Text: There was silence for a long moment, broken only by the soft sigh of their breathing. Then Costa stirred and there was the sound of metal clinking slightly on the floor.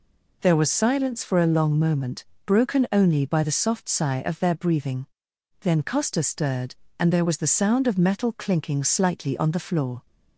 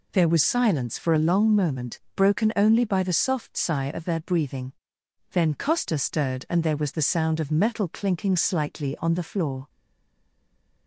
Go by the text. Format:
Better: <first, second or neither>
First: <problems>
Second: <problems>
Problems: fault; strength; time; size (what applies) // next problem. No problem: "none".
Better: first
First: none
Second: stays silent after the last word; noticeable; from 9.6 s on; 1.2 s long